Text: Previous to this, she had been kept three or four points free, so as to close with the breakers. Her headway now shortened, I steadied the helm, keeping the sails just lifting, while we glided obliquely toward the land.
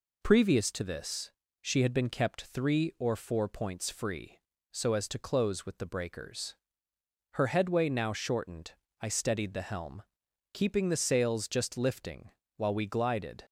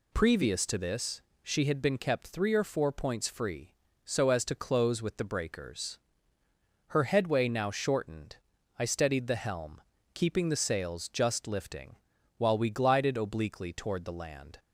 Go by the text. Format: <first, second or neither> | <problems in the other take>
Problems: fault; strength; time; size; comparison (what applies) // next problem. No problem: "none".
second | stops before "obliquely toward the land"; at 13.4 s